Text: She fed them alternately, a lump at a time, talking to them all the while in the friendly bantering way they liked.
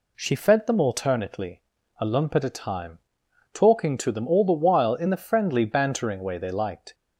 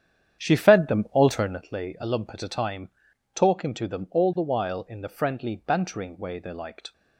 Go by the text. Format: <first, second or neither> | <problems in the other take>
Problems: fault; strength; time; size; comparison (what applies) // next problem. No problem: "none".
first | starts louder than the rest; strong; until 1.7 s; 9 dB